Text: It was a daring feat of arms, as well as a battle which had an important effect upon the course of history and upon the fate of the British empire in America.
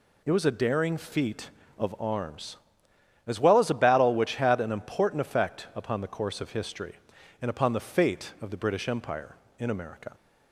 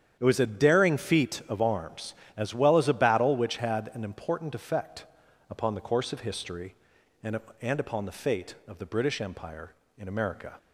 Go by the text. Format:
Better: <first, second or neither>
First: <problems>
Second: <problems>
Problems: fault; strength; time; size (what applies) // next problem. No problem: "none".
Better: first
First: none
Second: starts louder than the rest; strong; until 1.2 s; 9 dB // pauses between "effect" and "upon"; noticeable; at 5.0 s; 0.46 s long // says "and" twice; at 7.5 s